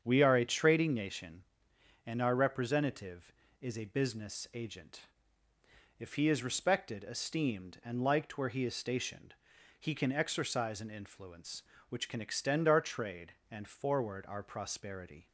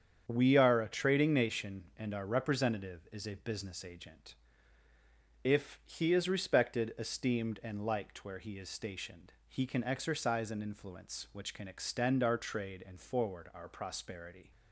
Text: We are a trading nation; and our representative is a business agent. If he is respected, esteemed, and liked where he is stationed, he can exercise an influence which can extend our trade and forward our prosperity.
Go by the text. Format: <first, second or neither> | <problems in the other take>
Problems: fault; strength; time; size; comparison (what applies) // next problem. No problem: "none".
neither | starts louder than the rest; strong; the same in both